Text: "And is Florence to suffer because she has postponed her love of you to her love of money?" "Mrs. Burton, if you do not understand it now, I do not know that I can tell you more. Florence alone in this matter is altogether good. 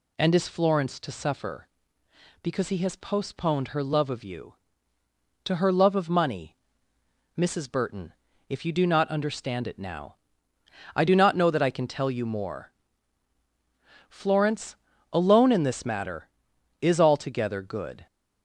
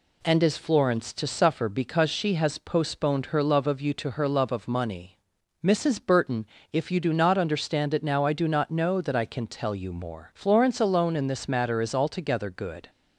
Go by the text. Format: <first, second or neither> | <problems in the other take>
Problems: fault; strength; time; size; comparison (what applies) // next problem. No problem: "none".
second | says "he" for "she"; at 2.6 s // pauses between "Florence" and "alone"; slight; at 14.7 s; 0.36 s long